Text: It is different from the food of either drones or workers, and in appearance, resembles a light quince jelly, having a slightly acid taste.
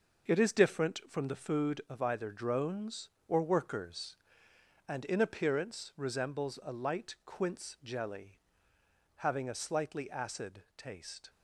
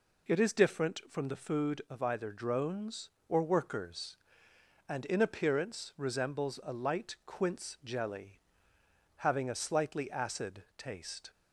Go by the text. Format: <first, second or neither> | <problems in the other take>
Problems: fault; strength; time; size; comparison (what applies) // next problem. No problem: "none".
second | gets quieter; strong; throughout; 7.5 dB